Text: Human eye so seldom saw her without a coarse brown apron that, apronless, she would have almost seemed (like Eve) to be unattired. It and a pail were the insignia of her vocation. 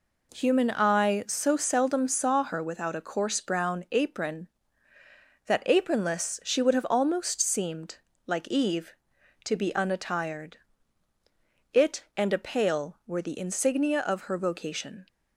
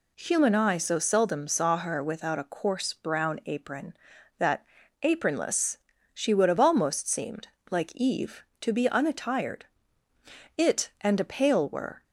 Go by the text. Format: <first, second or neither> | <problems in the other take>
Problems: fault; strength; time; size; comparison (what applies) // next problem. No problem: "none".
first | stops before "the insignia of her vocation"; at 12.0 s